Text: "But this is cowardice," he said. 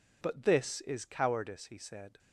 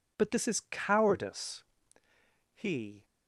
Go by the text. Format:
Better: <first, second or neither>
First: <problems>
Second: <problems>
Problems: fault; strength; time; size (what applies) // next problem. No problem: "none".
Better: first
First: none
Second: stops before "said"; at 3.0 s